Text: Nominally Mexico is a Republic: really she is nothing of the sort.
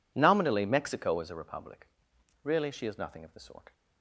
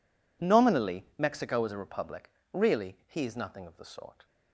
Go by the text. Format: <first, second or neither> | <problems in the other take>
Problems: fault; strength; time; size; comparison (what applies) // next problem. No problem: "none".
first | says "he" for "she"; at 3.0 s